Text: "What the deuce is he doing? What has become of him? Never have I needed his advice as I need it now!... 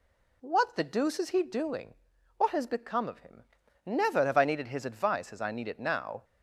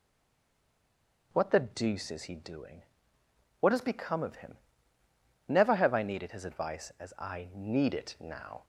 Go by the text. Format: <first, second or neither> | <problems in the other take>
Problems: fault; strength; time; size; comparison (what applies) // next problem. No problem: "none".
first | stays silent before the first word; noticeable; until 1.3 s; 1.3 s long // starts louder than the rest; until 2.3 s; 7 dB